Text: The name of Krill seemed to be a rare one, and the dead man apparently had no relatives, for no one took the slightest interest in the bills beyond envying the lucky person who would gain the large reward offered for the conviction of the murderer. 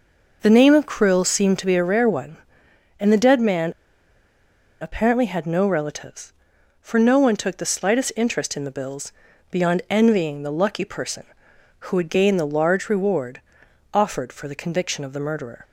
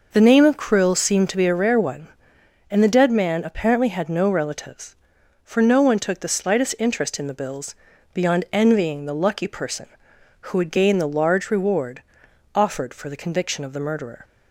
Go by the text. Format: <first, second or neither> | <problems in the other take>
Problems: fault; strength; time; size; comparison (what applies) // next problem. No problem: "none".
second | pauses between "man" and "apparently"; at 3.7 s; 1.0 s long // pauses between "bills" and "beyond"; slight; at 9.1 s; 0.36 s long; slight in the second // pauses between "reward" and "offered"; noticeable; at 13.3 s; 0.54 s long; noticeable in the second